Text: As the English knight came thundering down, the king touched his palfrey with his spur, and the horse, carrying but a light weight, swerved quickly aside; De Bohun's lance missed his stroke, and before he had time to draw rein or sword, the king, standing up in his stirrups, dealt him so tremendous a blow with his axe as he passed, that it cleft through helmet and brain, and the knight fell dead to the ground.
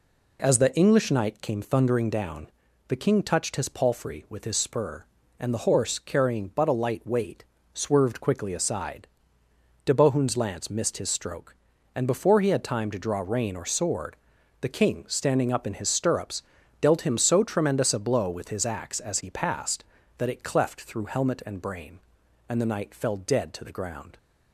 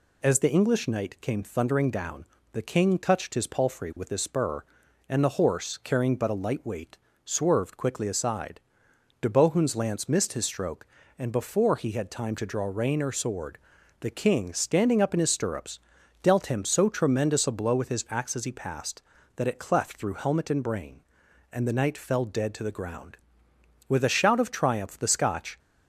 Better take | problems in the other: first | goes on to say "With a shout of triumph the Scotch"; strong; from 23.8 s on; 1.7 s long

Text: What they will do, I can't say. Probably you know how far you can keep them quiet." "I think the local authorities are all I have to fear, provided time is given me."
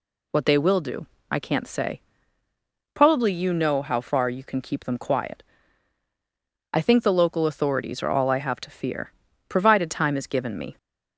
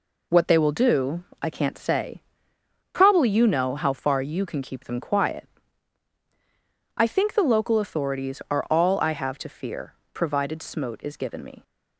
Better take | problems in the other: first | says "smote" for "time"; at 10.6 s

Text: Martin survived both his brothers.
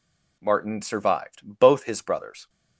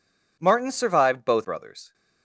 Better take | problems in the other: first | skips "his"; at 1.4 s

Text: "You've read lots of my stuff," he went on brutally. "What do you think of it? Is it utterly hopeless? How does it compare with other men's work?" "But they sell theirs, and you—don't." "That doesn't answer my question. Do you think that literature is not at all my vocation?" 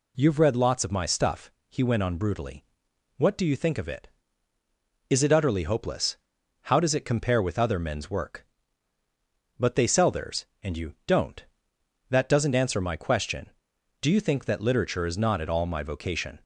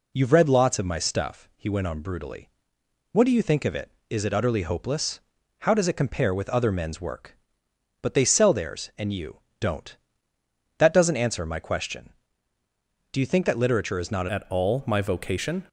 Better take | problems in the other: first | changes voice at "at"; from 14.2 s on; 1.4 s long

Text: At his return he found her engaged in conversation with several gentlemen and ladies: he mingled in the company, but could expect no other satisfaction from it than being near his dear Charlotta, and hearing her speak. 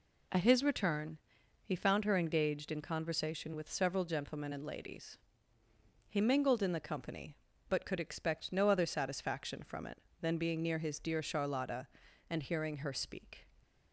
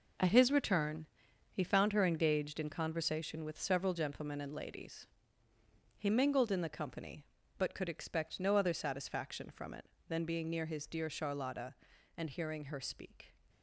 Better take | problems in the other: first | gets quieter; strong; throughout; 9 dB // pauses between "return" and "he"; noticeable; at 1.0 s; 0.46 s long; noticeable in the first

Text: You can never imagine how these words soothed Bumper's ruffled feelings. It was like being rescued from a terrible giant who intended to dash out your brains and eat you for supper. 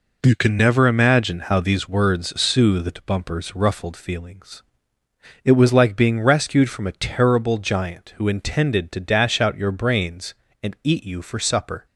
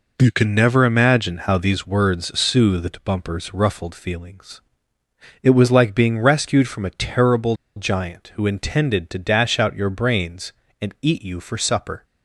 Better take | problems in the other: first | pauses between "terrible" and "giant"; slight; at 7.5 s; 0.20 s long

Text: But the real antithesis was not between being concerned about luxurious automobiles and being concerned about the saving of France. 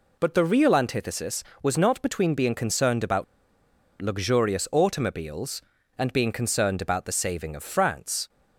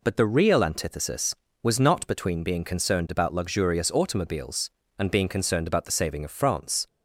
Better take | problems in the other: second | pauses between "about" and "luxurious"; noticeable; at 3.2 s; 0.77 s long

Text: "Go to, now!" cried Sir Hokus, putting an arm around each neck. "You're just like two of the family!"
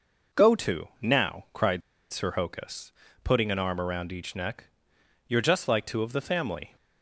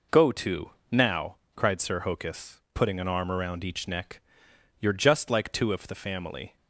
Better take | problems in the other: second | pauses between "cried" and "Sir"; slight; at 1.8 s; 0.32 s long

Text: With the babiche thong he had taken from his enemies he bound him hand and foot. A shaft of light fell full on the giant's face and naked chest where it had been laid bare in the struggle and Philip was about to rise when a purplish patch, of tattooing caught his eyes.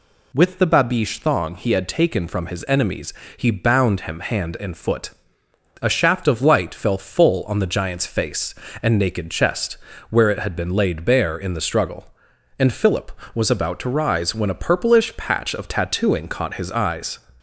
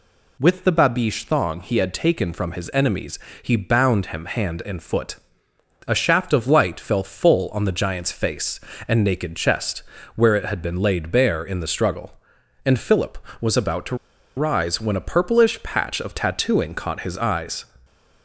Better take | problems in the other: first | pauses between "enemies" and "he"; slight; at 3.1 s; 0.22 s long; slight in the first // pauses between "chest" and "where"; slight; at 9.8 s; 0.34 s long; slight in the first // pauses between "to" and "rise"; at 13.9 s; 0.41 s long

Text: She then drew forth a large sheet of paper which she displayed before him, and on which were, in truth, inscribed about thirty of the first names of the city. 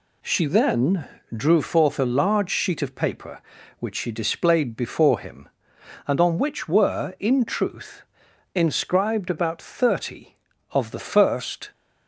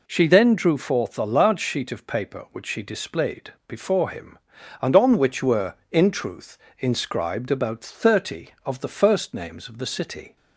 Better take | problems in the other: second | pauses between "then" and "drew"; slight; at 1.0 s; 0.26 s long // stops before "names of the city"; at 11.7 s

